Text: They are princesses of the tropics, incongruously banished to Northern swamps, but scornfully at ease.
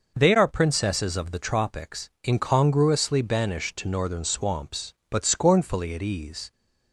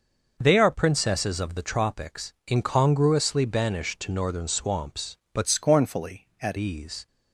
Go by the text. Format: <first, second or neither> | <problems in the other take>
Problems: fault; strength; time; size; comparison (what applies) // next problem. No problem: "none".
first | changes voice from "scornfully" to "at"; from 5.4 to 6.5 s; 1.1 s long